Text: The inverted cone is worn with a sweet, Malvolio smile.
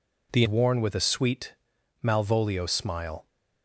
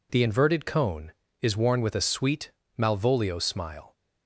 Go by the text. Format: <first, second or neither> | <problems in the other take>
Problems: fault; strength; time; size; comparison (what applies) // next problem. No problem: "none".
second | skips "inverted cone is"; at 0.4 s